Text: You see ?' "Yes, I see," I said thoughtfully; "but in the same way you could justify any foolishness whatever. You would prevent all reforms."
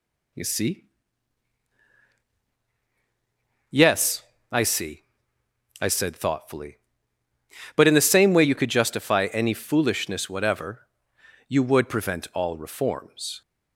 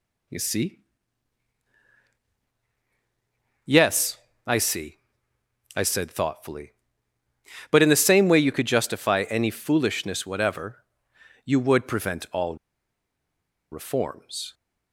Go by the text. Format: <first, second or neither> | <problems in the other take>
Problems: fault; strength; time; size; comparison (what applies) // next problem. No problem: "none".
first | pauses between "all" and "reforms"; at 12.5 s; 1.1 s long